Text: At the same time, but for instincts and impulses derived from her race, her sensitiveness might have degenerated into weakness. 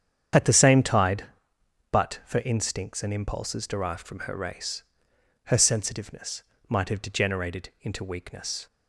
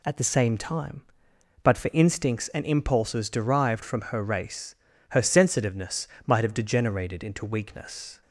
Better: second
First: starts louder than the rest; strong; until 2.0 s; 8.5 dB // says "tide" for "time"; at 0.8 s // pauses between "sensitiveness" and "might"; slight; at 6.4 s; 0.26 s long // pauses between "degenerated" and "into"; slight; at 7.6 s; 0.16 s long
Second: pauses between "sensitiveness" and "might"; slight; at 6.0 s; 0.18 s long

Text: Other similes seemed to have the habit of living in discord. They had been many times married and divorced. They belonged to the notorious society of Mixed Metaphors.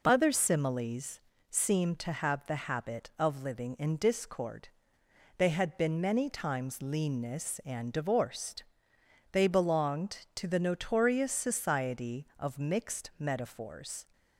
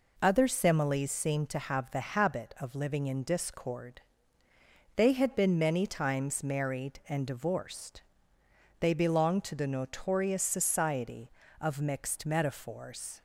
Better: second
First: pauses between "similes" and "seemed"; slight; at 1.2 s; 0.30 s long // says "leanness" for "married"; at 6.8 s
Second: none

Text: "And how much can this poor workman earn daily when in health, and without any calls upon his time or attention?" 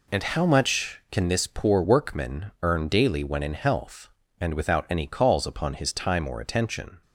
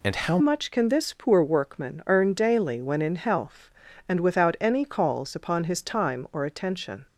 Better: first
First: none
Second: changes voice at "much"; from 0.3 s on; 6.7 s long

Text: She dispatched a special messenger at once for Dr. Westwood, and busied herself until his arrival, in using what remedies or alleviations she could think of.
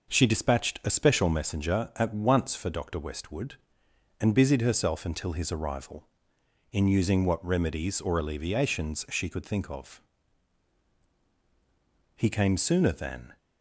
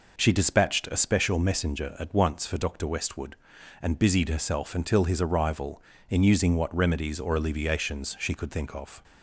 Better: second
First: goes on to say "He came sooner than"; noticeable; from 12.1 s on; 1.2 s long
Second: none

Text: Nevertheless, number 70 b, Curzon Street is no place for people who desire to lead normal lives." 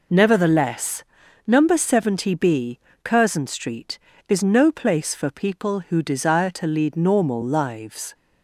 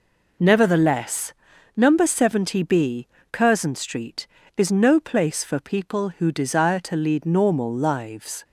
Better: neither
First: none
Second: none

